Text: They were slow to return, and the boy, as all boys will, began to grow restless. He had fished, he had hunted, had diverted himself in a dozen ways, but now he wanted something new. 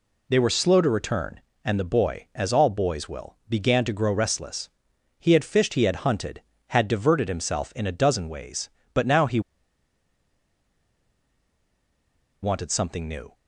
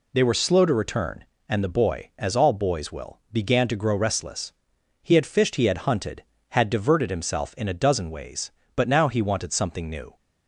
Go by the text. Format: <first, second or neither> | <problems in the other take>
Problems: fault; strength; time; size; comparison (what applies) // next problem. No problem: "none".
second | pauses between "he" and "wanted"; strong; at 9.4 s; 3.0 s long